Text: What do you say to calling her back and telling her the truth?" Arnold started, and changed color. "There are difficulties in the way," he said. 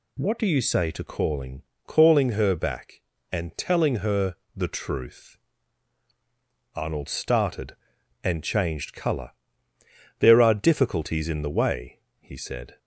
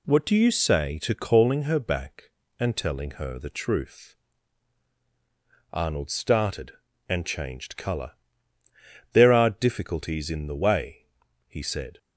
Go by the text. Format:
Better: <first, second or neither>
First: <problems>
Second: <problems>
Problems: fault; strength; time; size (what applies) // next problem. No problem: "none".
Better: second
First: says "calling" twice; at 1.8 s // pauses between "her" and "the"; slight; at 4.3 s; 0.22 s long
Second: none